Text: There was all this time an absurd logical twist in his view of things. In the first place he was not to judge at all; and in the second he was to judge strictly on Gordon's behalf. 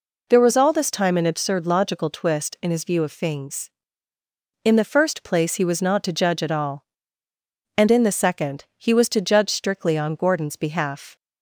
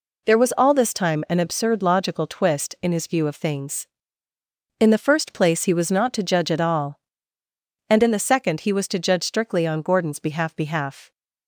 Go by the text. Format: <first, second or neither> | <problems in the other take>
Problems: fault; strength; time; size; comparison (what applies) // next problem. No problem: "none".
first | says "behalf" twice; at 10.5 s